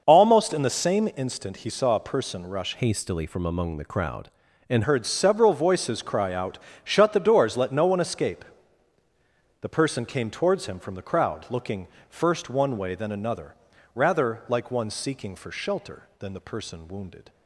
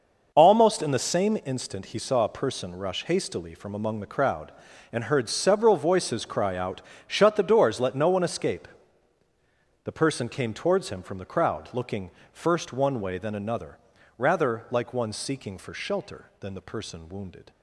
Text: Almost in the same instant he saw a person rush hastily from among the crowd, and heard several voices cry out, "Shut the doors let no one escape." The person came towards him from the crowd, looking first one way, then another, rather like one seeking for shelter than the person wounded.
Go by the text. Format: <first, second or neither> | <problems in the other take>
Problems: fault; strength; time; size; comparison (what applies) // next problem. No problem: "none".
second | changes voice from "hastily" to "and"; from 2.7 to 4.8 s; 2.1 s long // pauses between "looking" and "first"; slight; at 11.8 s; 0.22 s long; slight in the second